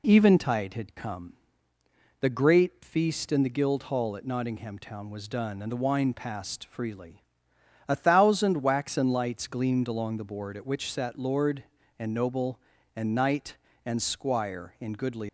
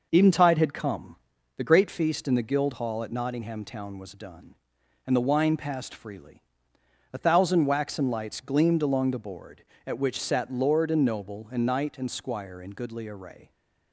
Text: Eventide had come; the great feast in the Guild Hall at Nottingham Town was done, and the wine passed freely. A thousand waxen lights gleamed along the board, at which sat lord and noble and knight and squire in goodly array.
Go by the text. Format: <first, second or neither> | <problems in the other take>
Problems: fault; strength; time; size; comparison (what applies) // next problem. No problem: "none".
second | stops before "array"; at 15.2 s